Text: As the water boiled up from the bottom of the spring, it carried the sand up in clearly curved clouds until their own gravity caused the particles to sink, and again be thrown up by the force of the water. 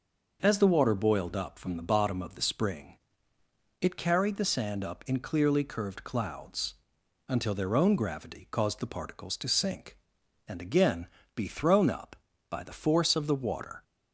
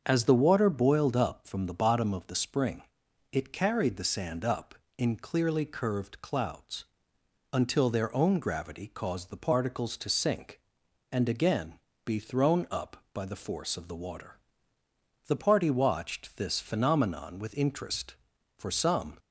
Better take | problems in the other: first | starts louder than the rest; until 1.0 s; 7 dB // pauses between "clouds" and "until"; noticeable; at 6.8 s; 0.68 s long; noticeable in the first // pauses between "again" and "be"; slight; at 11.7 s; 0.30 s long; slight in the first // goes on to say "The party watched this phenomenon with interest for some"; strong; from 15.2 s on; 3.9 s long

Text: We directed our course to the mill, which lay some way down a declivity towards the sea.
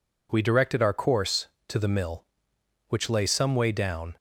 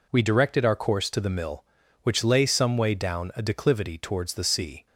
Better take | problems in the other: second | stops before "a declivity towards the sea"; at 4.1 s

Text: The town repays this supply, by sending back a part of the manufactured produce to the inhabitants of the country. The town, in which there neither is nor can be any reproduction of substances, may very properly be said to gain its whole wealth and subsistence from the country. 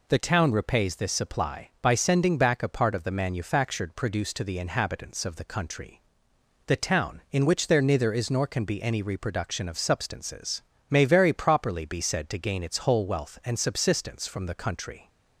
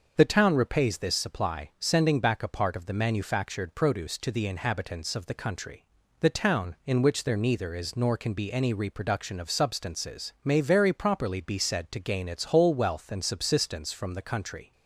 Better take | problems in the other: first | starts louder than the rest; until 1.1 s; 6 dB // skips "by"; at 1.7 s

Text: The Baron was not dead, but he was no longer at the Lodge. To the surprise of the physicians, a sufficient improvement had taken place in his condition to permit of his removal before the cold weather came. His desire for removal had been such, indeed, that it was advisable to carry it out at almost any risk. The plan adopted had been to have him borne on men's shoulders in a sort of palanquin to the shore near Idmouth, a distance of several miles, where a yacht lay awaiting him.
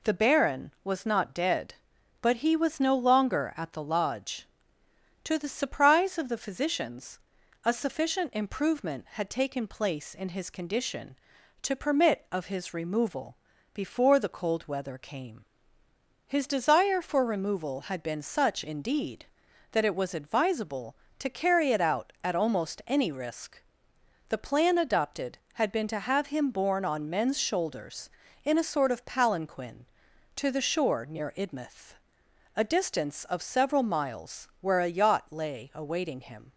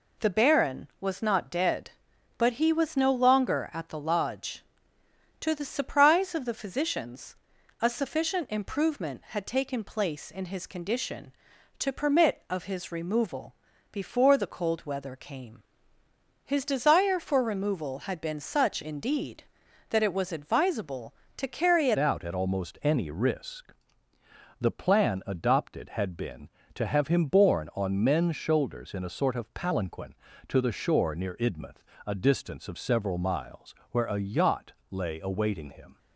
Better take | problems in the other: first | pauses between "removal" and "before"; at 13.5 s; 0.38 s long; also in the first // changes voice at "out"; from 21.9 s on; 14.0 s long // pauses between "yacht" and "lay"; slight; at 34.7 s; 0.18 s long

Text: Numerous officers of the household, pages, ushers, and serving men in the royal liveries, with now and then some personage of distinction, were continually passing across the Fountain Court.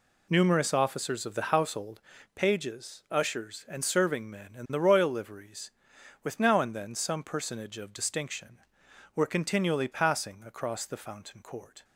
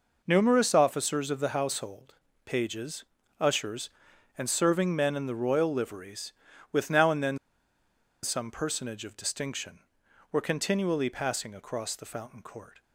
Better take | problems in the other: first | pauses between "then" and "some"; noticeable; at 7.3 s; 0.87 s long

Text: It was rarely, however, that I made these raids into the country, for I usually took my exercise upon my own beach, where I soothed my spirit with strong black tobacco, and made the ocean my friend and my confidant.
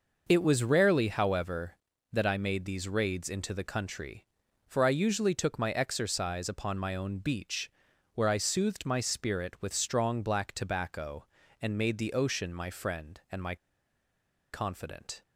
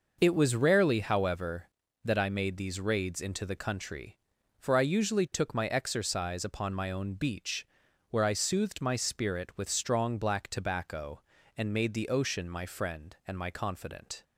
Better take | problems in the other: second | pauses between "my" and "confidant"; noticeable; at 13.5 s; 0.96 s long

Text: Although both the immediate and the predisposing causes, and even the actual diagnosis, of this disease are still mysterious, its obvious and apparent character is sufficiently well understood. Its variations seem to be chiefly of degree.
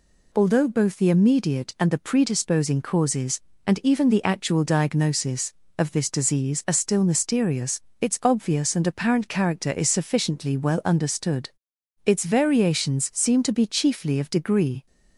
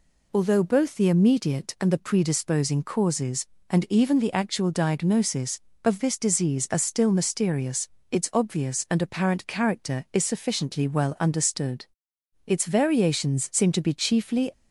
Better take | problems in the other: first | stops before "of degree"; at 14.5 s

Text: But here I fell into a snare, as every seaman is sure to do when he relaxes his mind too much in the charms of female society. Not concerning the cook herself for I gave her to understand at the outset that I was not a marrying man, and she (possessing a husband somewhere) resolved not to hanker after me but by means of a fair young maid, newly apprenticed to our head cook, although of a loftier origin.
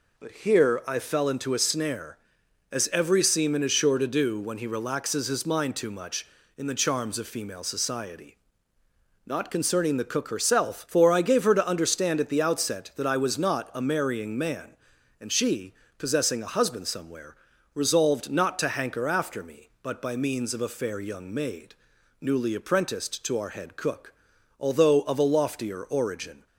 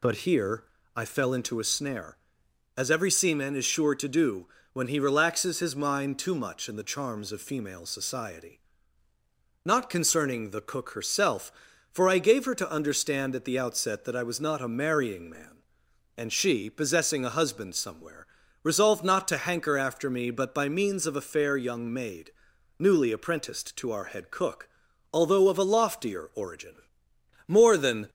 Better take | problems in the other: first | pauses between "here" and "I"; slight; at 0.6 s; 0.34 s long // pauses between "do" and "when"; slight; at 4.4 s; 0.26 s long // goes on to say "More than"; noticeable; from 27.4 s on; 0.62 s long

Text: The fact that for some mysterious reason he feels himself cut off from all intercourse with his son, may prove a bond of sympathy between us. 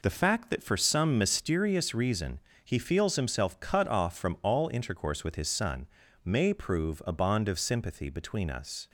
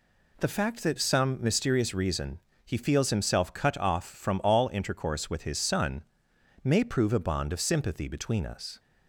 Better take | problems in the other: first | skips "for"; at 0.9 s // pauses between "reason" and "he"; slight; at 2.3 s; 0.26 s long; slight in the first

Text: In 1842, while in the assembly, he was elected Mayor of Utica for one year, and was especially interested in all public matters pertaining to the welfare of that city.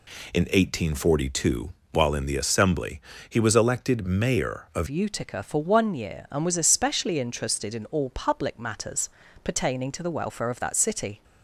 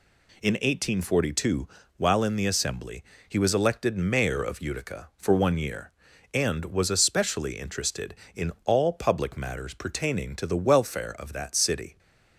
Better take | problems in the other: second | changes voice at "Utica"; from 4.8 s on; 6.4 s long // pauses between "matters" and "pertaining"; slight; at 9.0 s; 0.34 s long

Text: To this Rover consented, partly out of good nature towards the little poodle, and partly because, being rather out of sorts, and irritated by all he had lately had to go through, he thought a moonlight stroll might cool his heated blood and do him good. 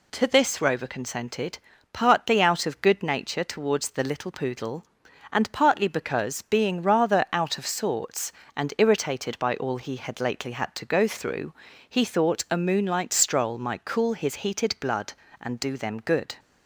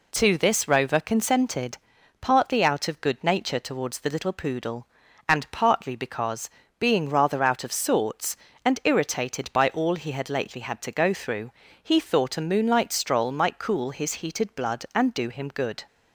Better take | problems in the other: second | says "them" for "him"; at 15.7 s

